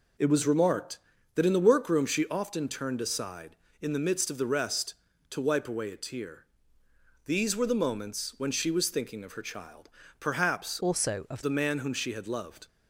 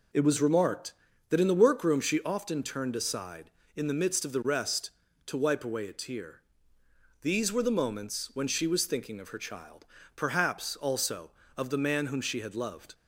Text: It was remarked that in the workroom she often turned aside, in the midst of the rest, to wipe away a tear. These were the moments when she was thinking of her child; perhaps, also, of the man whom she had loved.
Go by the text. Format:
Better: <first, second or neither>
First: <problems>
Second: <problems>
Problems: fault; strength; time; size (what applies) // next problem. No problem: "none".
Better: second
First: changes voice from "also" to "of"; from 10.8 to 11.4 s; 0.6 s long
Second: none